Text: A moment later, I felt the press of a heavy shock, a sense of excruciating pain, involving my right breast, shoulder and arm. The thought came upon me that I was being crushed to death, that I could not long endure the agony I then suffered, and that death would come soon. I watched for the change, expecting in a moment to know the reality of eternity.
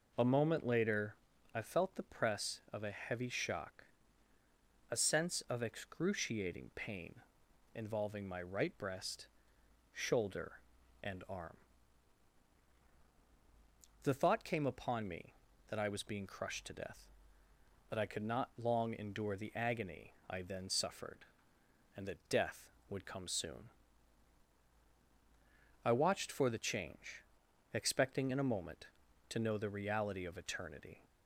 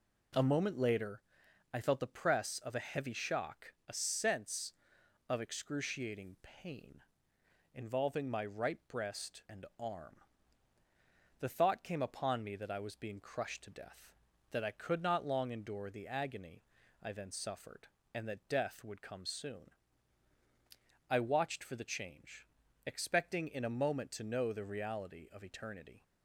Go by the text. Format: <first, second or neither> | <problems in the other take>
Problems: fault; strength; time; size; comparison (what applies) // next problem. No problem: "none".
first | skips "shoulder"; at 9.4 s // pauses between "agony" and "I"; at 16.6 s; 0.40 s long; slight in the first